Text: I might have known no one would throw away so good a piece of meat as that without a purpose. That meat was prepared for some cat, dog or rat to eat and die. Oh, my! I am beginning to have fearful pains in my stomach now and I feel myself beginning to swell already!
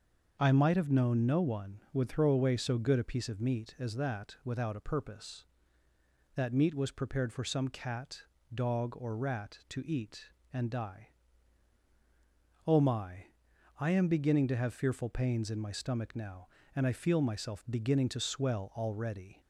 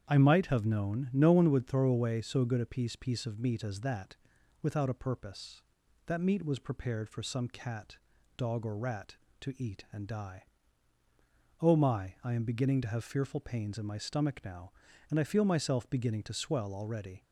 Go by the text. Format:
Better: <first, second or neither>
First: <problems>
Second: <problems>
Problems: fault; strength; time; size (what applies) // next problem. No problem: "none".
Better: first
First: starts louder than the rest; until 1.4 s; 6.5 dB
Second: starts louder than the rest; strong; until 1.0 s; 8.5 dB // says "piece" twice; at 2.9 s // pauses between "that" and "without"; at 4.1 s; 0.44 s long